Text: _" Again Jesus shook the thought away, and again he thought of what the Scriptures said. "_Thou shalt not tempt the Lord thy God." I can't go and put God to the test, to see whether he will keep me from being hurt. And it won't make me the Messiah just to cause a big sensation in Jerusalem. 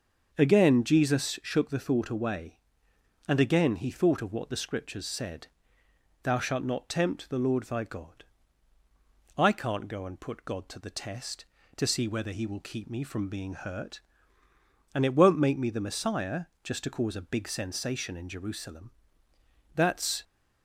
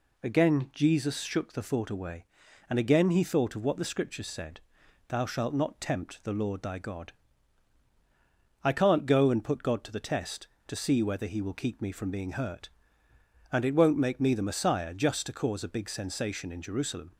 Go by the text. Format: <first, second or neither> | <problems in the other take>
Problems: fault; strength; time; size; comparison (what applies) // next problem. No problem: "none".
second | starts louder than the rest; until 1.3 s; 6.5 dB // pauses between "Messiah" and "just"; slight; at 16.4 s; 0.18 s long // goes on to say "That's"; slight; from 19.7 s on; 0.48 s long